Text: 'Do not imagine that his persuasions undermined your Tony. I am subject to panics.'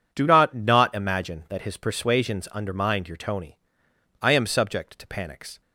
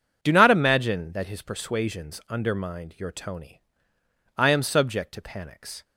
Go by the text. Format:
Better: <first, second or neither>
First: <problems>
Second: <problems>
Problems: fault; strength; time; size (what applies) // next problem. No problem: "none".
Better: second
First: says "not" twice; at 0.5 s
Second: none